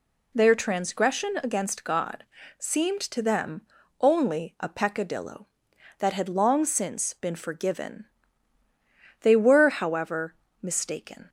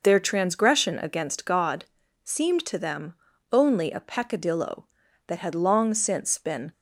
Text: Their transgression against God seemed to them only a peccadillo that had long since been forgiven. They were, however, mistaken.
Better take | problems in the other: first | pauses between "God" and "seemed"; at 1.8 s; 0.40 s long; slight in the first // pauses between "them" and "only"; slight; at 3.1 s; 0.36 s long; also in the first // stops before "forgiven They were however mistaken"; at 6.7 s

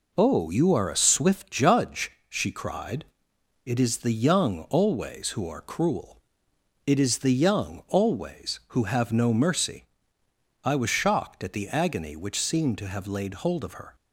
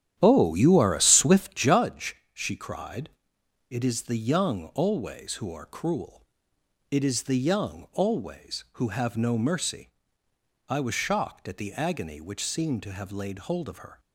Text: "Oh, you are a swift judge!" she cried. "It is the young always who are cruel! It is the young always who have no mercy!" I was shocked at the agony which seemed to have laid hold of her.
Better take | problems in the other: first | starts louder than the rest; strong; until 1.8 s; 10.5 dB

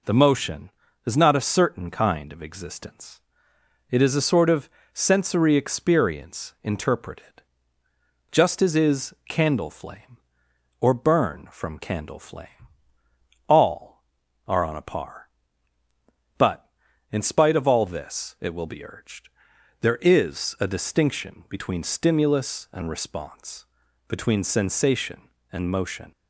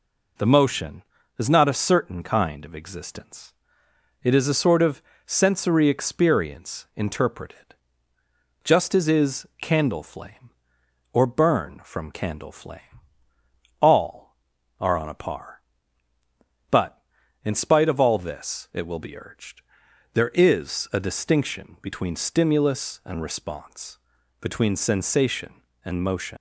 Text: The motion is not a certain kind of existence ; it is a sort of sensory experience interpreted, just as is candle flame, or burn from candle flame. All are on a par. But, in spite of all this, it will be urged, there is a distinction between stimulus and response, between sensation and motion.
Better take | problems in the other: first | pauses between "of" and "sensory"; slight; at 5.0 s; 0.24 s long; slight in the first // pauses between "is" and "candle"; slight; at 9.4 s; 0.16 s long; slight in the first // leaves "motion" unfinished; at 26.3 s; 70 ms

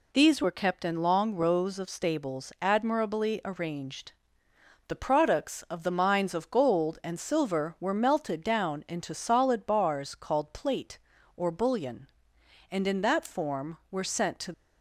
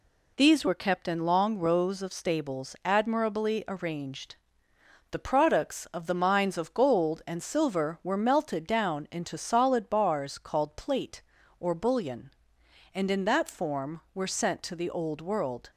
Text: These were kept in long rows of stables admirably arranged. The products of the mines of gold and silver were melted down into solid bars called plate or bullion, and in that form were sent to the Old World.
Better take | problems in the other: second | stops before "the Old World"; at 14.5 s

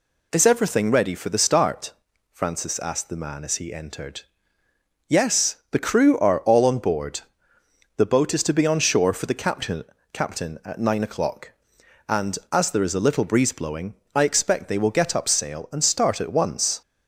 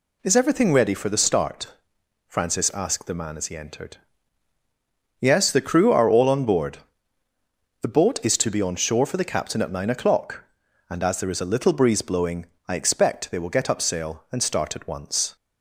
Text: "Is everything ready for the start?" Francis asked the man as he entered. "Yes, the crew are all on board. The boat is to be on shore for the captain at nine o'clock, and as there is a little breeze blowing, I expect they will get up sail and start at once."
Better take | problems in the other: second | says "captain" twice; at 10.1 s

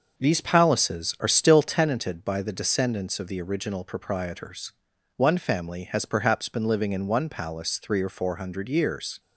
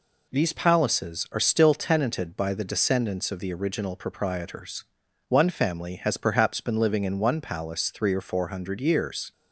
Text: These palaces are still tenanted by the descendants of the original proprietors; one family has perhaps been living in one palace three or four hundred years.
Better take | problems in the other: second | starts louder than the rest; until 1.9 s; 6 dB

